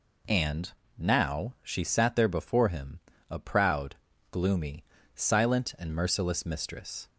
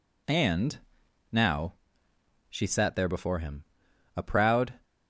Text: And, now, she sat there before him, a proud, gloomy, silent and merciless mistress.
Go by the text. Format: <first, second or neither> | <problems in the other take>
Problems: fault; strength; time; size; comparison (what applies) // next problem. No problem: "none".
first | stops before "gloomy silent and merciless mistress"; at 4.8 s